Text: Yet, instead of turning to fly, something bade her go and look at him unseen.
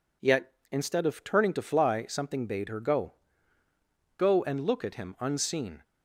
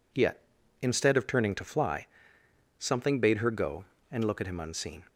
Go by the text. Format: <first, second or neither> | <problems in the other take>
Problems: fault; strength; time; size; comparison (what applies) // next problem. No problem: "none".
second | says "go" twice; at 4.1 s